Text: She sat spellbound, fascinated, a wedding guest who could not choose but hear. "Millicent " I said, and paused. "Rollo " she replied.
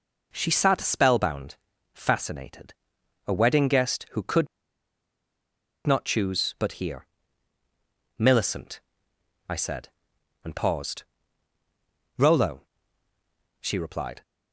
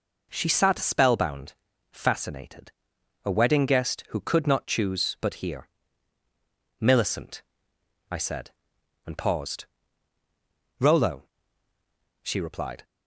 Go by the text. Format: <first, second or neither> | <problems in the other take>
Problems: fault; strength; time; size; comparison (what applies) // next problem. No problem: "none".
second | pauses between "could" and "not"; strong; at 4.4 s; 1.3 s long